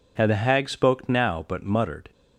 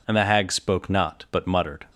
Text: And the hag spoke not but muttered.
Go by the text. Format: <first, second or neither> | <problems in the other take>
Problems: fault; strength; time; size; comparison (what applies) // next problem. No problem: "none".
second | says "now" for "not"; at 1.1 s